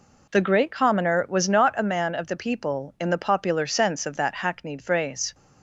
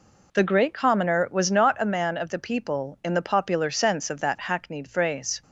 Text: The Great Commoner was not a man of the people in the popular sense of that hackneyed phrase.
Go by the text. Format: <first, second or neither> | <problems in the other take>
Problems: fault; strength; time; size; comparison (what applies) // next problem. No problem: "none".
neither | none